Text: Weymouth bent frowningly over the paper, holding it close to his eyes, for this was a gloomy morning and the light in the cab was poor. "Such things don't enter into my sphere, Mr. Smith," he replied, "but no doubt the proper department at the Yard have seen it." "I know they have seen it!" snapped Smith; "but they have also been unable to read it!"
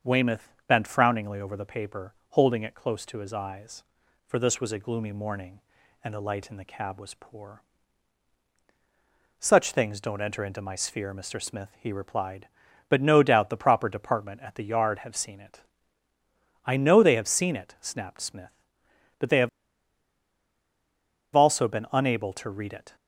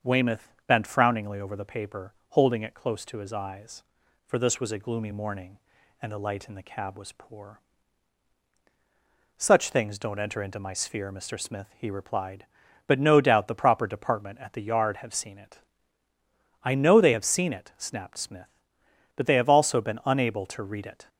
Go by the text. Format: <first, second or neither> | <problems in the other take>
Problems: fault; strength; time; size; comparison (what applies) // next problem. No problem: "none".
second | starts louder than the rest; until 1.1 s; 7 dB; also in the second // pauses between "have" and "also"; strong; at 19.4 s; 1.8 s long